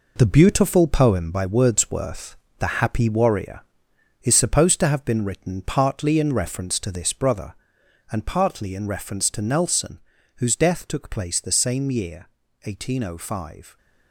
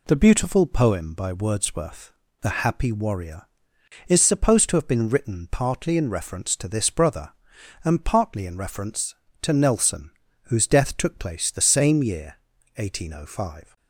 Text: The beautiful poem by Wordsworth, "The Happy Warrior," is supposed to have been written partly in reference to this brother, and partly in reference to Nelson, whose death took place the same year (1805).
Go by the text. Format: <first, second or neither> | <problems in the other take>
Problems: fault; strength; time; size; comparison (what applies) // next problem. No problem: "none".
second | gets quieter; strong; throughout; 8.5 dB